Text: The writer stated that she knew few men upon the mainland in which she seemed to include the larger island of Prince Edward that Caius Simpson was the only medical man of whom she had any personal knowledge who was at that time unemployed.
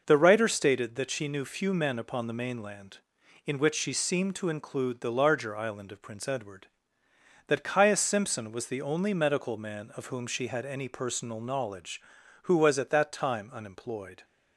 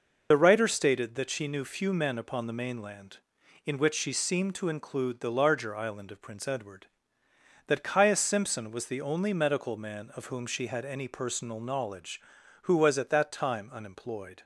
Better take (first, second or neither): first